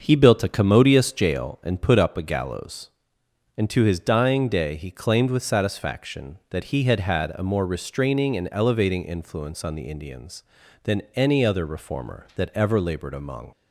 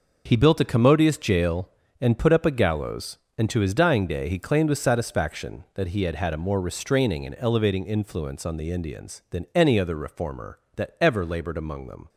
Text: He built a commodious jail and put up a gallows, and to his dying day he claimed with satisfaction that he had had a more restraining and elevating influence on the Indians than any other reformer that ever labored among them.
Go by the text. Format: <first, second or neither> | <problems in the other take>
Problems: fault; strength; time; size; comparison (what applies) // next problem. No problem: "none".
second | starts louder than the rest; until 1.0 s; 6.5 dB // stops before "them"; at 13.5 s